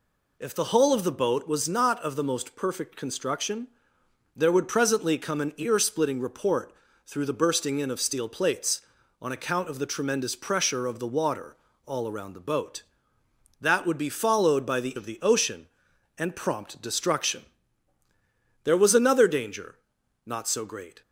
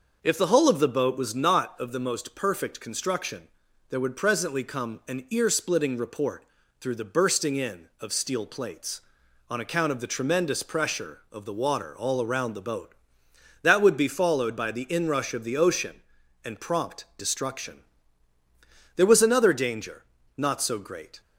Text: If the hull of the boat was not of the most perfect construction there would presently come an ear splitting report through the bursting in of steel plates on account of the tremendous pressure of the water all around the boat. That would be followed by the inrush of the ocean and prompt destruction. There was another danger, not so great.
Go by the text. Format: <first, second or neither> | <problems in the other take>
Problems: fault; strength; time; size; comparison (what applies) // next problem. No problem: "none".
second | pauses between "construction" and "there"; noticeable; at 3.6 s; 0.68 s long; also in the second // pauses between "report" and "through"; slight; at 6.7 s; 0.34 s long; slight in the second // pauses between "water" and "all"; slight; at 11.5 s; 0.30 s long // skips "inrush"; at 14.9 s